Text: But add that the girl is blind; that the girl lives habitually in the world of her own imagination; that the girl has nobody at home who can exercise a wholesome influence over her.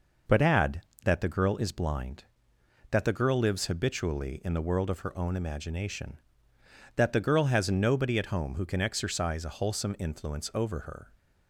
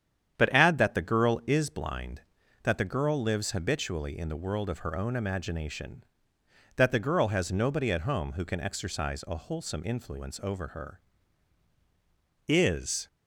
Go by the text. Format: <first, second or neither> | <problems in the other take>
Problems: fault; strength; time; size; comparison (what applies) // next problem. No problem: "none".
first | starts louder than the rest; strong; until 1.4 s; 9 dB // goes on to say "Is"; from 12.4 s on; 0.58 s long